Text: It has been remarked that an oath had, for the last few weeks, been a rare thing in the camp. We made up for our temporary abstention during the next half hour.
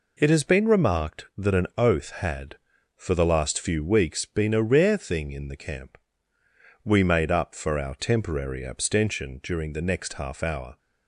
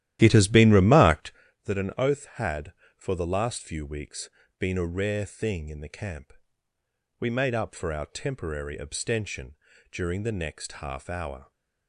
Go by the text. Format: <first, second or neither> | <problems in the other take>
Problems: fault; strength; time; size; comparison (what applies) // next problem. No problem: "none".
first | starts louder than the rest; strong; until 1.5 s; 13 dB // pauses between "abstention" and "during"; slight; at 9.5 s; 0.36 s long